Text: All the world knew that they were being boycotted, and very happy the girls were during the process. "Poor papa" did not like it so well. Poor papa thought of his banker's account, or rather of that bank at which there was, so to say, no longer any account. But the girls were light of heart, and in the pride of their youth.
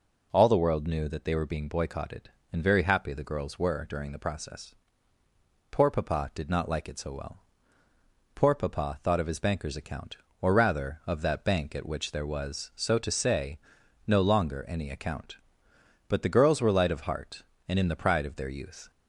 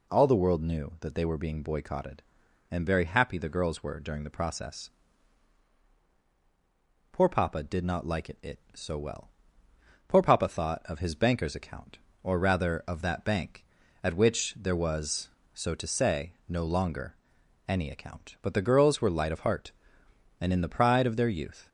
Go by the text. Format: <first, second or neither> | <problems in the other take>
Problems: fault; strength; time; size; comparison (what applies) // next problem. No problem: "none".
first | says "it" twice; at 8.4 s // pauses between "longer" and "any"; noticeable; at 17.1 s; 0.54 s long